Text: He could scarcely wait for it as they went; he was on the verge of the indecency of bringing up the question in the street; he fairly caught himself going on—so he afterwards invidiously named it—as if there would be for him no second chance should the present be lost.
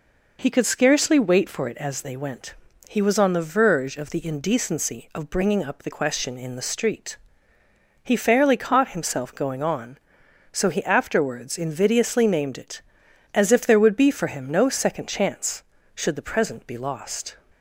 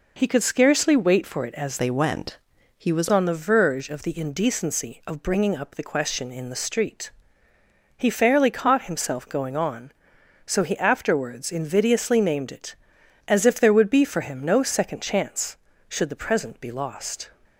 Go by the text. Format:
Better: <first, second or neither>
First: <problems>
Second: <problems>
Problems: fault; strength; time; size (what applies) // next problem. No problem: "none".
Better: first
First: none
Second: changes voice from "they" to "was"; from 1.7 to 3.0 s; 1.3 s long